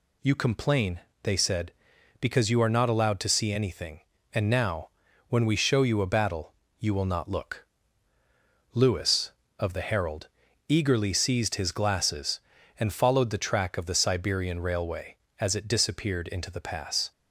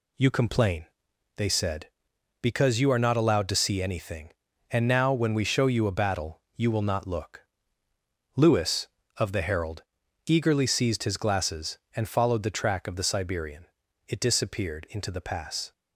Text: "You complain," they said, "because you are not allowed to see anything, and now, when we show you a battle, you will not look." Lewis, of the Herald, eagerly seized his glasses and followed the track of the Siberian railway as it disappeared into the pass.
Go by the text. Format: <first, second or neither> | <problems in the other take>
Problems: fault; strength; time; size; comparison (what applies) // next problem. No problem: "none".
first | skips "railway as"; at 13.8 s